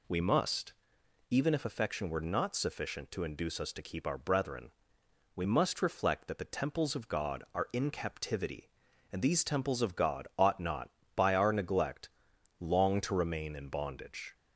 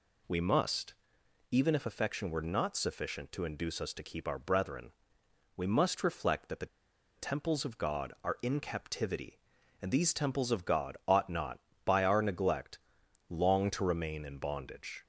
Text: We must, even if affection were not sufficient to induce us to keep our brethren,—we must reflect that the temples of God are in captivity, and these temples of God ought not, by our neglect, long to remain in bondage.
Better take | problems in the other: first | pauses between "the" and "temples"; noticeable; at 6.6 s; 0.50 s long

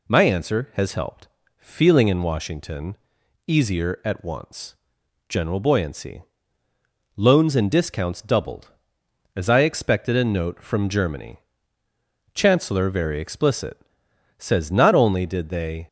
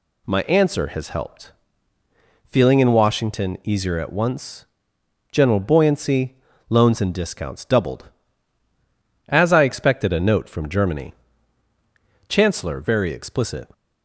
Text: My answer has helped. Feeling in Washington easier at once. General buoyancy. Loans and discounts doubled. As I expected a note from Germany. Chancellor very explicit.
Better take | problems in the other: second | pauses between "Washington" and "easier"; noticeable; at 2.9 s; 0.50 s long // goes on to say "Says not only did they"; from 14.3 s on; 1.5 s long

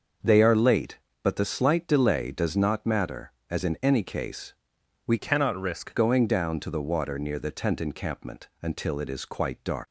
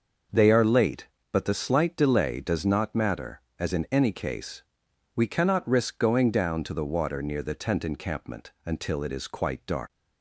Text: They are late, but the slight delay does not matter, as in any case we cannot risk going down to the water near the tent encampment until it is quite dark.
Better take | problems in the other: second | starts louder than the rest; until 1.4 s; 6.5 dB; noticeable in the second // pauses between "case" and "we"; noticeable; at 4.5 s; 0.54 s long; noticeable in the second // changes voice from "cannot" to "risk"; from 5.1 to 5.9 s; 0.8 s long

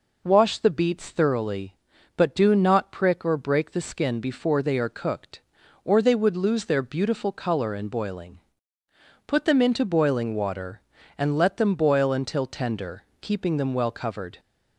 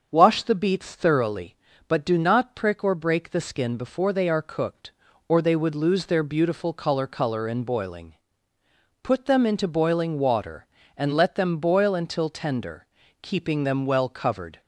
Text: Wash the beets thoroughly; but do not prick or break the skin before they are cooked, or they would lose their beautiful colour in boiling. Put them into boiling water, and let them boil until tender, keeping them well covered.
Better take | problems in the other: first | starts louder than the rest; until 1.1 s; 6.5 dB // says "colour" twice; at 7.0 s

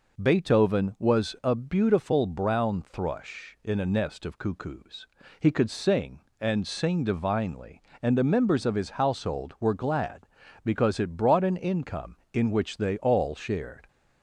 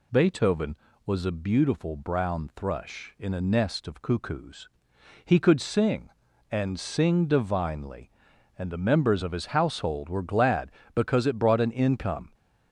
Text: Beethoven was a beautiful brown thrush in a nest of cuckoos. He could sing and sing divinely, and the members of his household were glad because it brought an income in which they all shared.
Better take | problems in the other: first | stops before "in which they all shared"; at 12.3 s

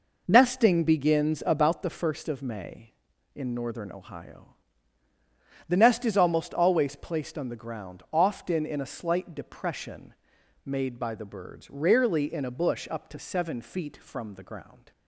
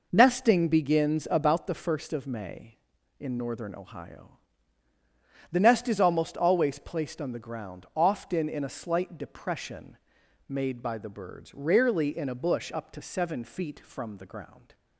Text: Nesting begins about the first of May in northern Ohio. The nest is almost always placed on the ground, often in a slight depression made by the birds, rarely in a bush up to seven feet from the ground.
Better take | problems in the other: neither | pauses between "depression" and "made"; noticeable; the same in both

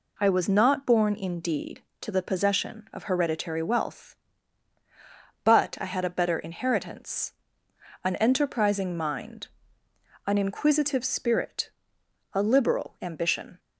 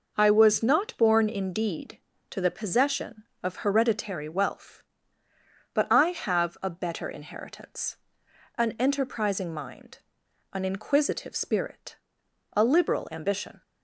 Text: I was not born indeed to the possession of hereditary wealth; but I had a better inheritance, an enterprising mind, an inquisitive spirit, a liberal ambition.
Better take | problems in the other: first | says "have" for "had"; at 6.0 s

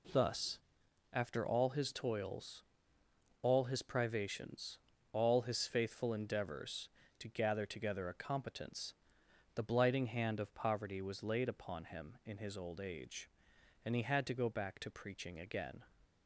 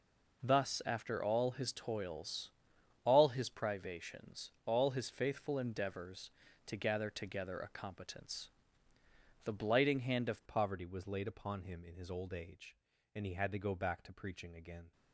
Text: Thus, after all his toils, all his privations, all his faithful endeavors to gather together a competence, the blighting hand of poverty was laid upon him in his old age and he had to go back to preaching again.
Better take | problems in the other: first | changes voice at "poverty"; from 10.4 s on; 4.5 s long

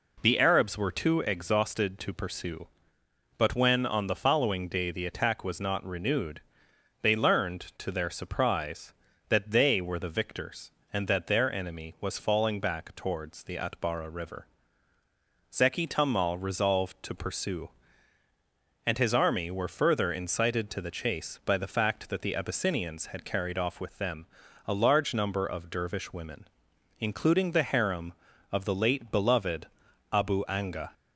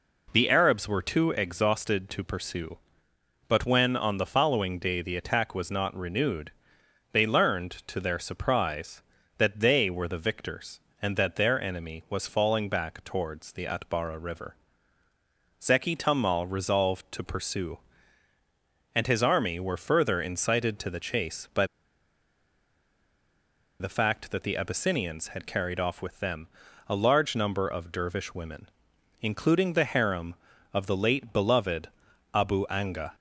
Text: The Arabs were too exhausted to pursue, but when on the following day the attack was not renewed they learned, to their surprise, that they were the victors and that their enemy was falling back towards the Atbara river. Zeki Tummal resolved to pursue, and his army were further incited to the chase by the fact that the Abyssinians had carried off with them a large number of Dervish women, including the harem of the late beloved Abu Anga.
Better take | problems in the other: first | pauses between "renewed" and "they"; noticeable; at 6.5 s; 0.60 s long; noticeable in the first // pauses between "by" and "the"; strong; at 21.6 s; 2.1 s long // pauses between "them" and "a"; at 26.4 s; 0.40 s long; also in the first // pauses between "beloved" and "Abu"; at 31.8 s; 0.44 s long; also in the first

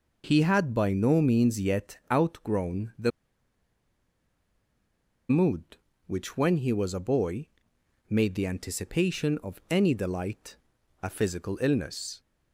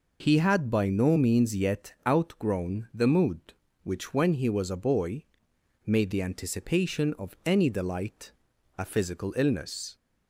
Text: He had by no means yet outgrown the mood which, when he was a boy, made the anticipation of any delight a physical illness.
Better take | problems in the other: second | pauses between "the" and "mood"; strong; at 3.1 s; 2.1 s long // pauses between "delight" and "a"; at 10.5 s; 0.44 s long; also in the second

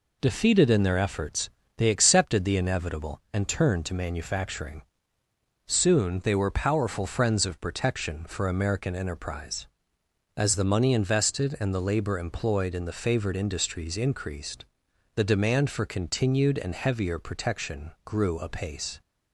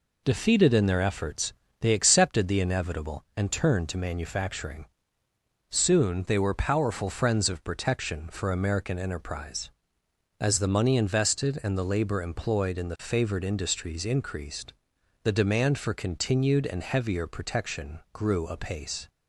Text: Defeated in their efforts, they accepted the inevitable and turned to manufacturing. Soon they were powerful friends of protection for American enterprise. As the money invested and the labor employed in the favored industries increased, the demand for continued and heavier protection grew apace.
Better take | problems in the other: neither | none

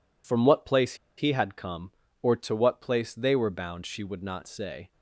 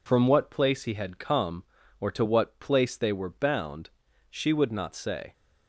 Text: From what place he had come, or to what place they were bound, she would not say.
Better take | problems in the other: second | pauses between "place" and "he"; slight; at 0.9 s; 0.24 s long

